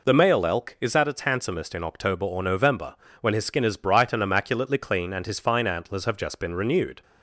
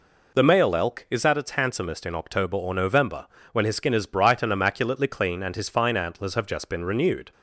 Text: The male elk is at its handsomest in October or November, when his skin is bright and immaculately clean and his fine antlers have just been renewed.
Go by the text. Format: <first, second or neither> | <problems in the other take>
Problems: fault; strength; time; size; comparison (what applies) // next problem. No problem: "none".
neither | none